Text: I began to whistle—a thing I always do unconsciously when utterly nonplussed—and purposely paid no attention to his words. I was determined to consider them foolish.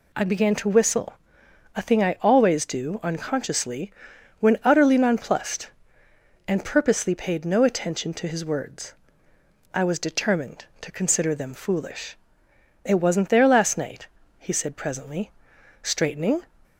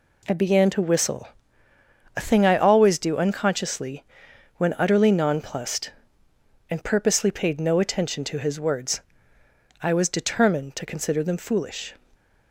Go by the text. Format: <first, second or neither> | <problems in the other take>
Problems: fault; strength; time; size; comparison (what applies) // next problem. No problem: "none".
second | pauses between "unconsciously" and "when"; noticeable; at 3.9 s; 0.48 s long; noticeable in the second // goes on to say "It wasn't there last night he said presently straightening"; strong; from 12.8 s on; 3.5 s long